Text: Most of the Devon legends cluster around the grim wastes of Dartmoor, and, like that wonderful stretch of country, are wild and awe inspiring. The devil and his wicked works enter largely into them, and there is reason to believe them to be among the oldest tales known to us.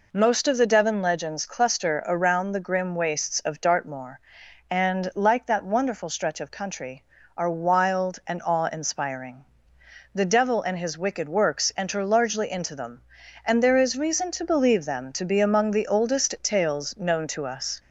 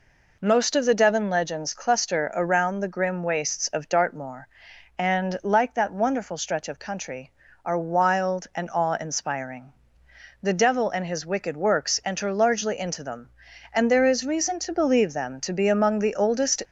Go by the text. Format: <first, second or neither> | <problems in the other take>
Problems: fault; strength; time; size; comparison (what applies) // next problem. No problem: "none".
first | stops before "tales known to us"; at 16.6 s